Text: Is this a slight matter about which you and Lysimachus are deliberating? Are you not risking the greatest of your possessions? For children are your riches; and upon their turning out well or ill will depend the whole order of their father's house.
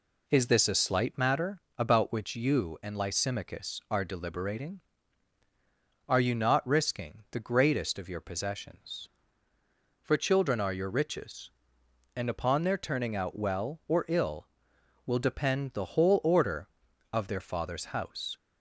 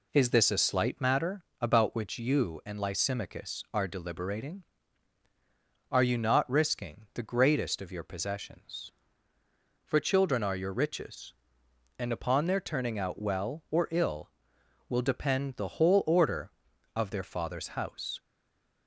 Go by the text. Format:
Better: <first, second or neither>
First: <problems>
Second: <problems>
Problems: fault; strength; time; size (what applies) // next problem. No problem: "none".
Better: first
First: pauses between "matter" and "about"; slight; at 1.6 s; 0.18 s long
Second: pauses between "matter" and "about"; slight; at 1.4 s; 0.18 s long // stays silent after the last word; slight; from 18.1 s on; 0.7 s long